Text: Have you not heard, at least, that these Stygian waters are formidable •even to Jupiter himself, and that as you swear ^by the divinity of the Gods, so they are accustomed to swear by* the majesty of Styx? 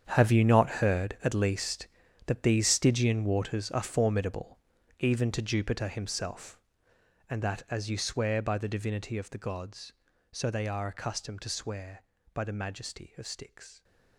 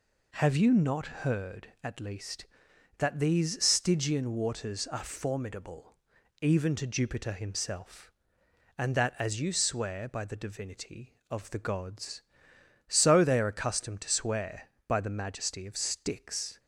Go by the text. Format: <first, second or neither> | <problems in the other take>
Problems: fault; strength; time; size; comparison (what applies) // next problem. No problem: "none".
second | gets quieter; strong; throughout; 14.5 dB